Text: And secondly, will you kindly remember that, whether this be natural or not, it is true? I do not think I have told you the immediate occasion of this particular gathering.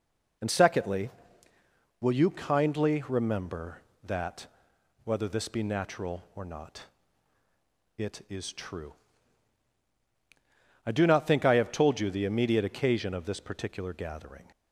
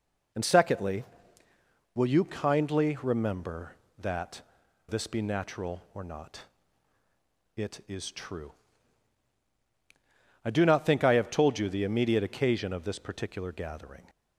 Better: first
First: none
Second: skips "whether"; at 4.6 s

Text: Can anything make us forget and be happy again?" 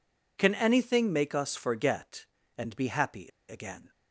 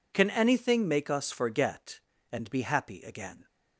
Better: second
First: pauses between "happy" and "again"; slight; at 3.2 s; 0.20 s long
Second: none

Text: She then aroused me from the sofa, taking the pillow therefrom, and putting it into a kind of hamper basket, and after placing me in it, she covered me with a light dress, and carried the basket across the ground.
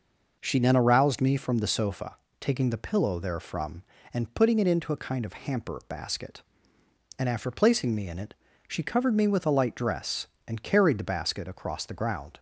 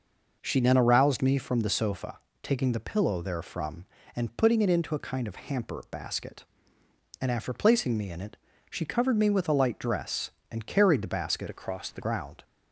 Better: first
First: none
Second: changes voice from "across" to "the"; from 11.4 to 12.0 s; 0.6 s long

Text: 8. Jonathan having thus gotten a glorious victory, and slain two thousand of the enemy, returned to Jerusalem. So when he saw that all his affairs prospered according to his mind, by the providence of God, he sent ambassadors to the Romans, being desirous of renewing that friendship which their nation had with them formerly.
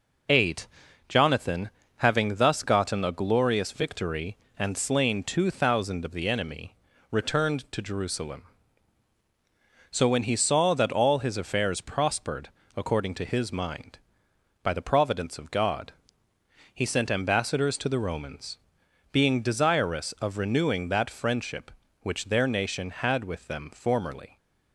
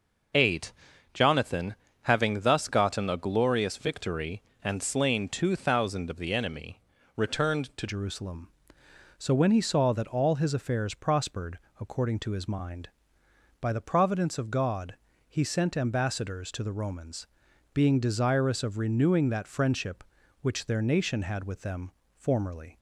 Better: first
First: pauses between "Jonathan" and "having"; slight; at 1.6 s; 0.30 s long // pauses between "prospered" and "according"; slight; at 12.4 s; 0.26 s long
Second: pauses between "Jonathan" and "having"; slight; at 1.7 s; 0.30 s long // changes voice at "Jerusalem"; from 7.8 s on; 14.9 s long // pauses between "prospered" and "according"; slight; at 11.5 s; 0.22 s long // pauses between "them" and "formerly"; slight; at 21.9 s; 0.24 s long

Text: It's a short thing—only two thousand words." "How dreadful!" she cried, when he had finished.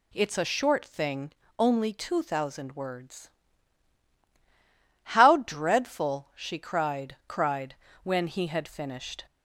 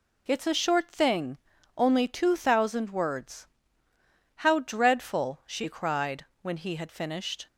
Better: second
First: says "cried" twice; at 7.2 s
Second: none

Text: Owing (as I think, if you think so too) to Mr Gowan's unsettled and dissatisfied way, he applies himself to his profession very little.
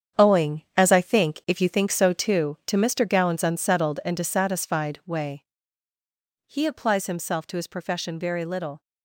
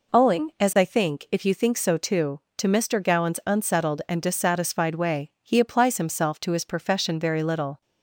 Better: second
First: gets quieter; strong; throughout; 10 dB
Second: none

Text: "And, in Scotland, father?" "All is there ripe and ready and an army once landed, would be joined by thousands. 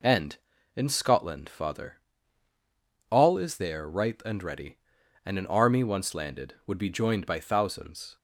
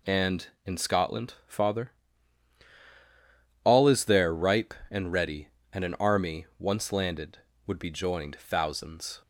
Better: first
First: none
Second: skips "by"; at 8.3 s

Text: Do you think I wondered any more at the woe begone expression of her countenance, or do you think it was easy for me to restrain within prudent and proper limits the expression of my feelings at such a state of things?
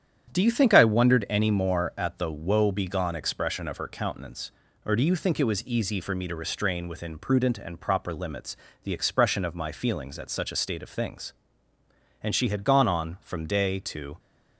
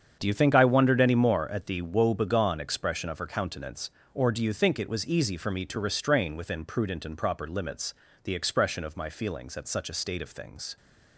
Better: second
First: starts louder than the rest; strong; until 1.3 s; 9.5 dB // pauses between "limits" and "the"; slight; at 8.5 s; 0.28 s long // goes on to say "And she had gone on from day to"; strong; from 12.2 s on; 1.9 s long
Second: starts louder than the rest; strong; until 1.2 s; 7.5 dB // pauses between "limits" and "the"; slight; at 7.9 s; 0.30 s long

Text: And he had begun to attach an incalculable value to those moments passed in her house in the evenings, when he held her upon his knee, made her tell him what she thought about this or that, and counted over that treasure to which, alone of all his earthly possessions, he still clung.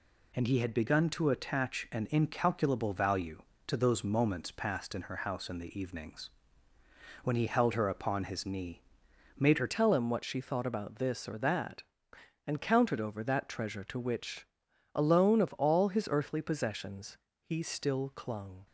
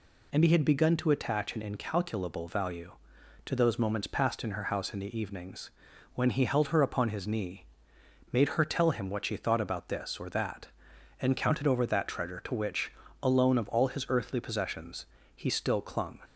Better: second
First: changes voice at "tell"; from 9.6 s on; 9.0 s long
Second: none

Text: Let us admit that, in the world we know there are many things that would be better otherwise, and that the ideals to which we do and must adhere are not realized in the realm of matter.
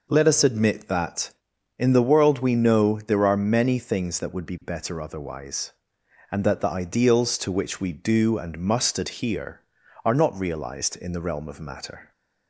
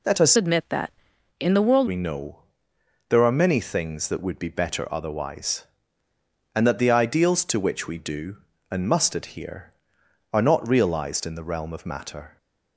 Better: first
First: none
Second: changes voice from "admit" to "world"; from 0.3 to 1.8 s; 1.5 s long // pauses between "know" and "there"; noticeable; at 2.3 s; 0.68 s long

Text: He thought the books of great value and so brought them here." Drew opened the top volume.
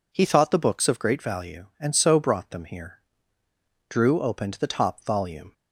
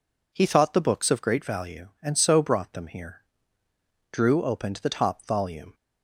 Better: neither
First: none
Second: none

